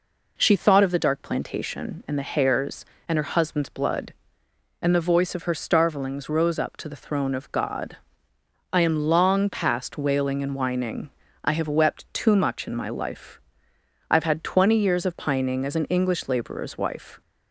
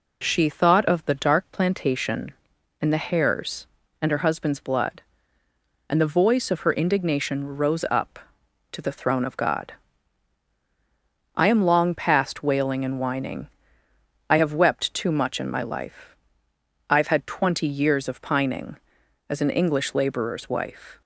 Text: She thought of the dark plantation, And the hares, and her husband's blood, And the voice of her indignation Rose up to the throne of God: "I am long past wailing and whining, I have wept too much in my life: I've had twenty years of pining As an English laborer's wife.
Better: second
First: says "starvelings" for "indignation"; at 5.5 s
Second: none

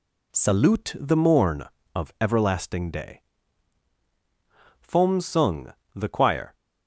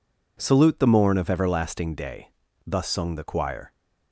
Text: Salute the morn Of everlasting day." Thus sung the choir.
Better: second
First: says "Fom" for "Thus"; at 4.8 s // pauses between "sung" and "the"; slight; at 5.7 s; 0.22 s long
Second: none

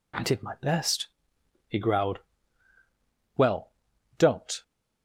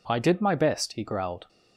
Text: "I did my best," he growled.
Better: second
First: goes on to say "Well don't"; noticeable; from 3.3 s on; 1.2 s long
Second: none

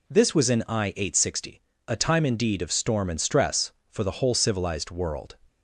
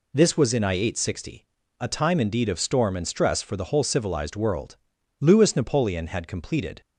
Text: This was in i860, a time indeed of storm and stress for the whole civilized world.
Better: first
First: none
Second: goes on to say "Louis Napoleon had completed"; from 5.2 s on; 1.6 s long

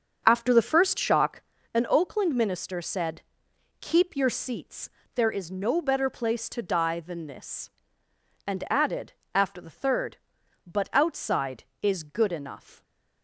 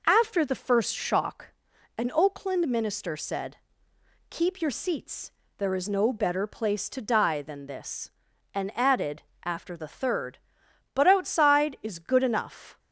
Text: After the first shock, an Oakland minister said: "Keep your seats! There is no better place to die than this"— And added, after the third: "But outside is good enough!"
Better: second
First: starts louder than the rest; until 1.5 s; 6 dB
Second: none

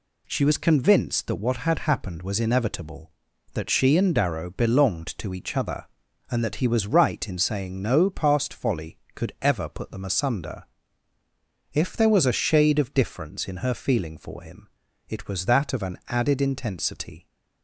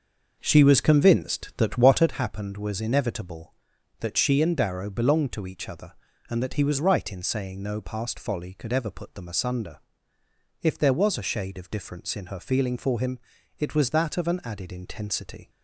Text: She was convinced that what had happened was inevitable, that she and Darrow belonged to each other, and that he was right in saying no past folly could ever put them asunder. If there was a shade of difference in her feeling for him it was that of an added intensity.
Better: first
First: pauses between "him" and "it"; at 14.6 s; 0.40 s long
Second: starts louder than the rest; noticeable; until 2.2 s; 6 dB // pauses between "him" and "it"; at 13.1 s; 0.38 s long

